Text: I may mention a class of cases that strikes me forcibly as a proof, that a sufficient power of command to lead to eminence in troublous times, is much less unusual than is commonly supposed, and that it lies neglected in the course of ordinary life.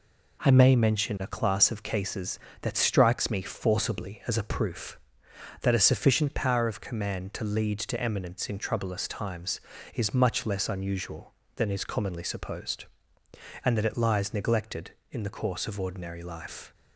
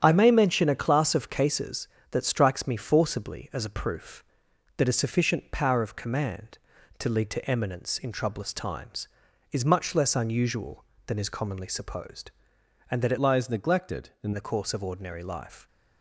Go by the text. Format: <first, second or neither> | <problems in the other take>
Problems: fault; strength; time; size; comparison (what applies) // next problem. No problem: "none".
first | starts louder than the rest; strong; until 1.0 s; 9 dB // changes voice from "lies" to "in"; from 13.1 to 14.3 s; 1.2 s long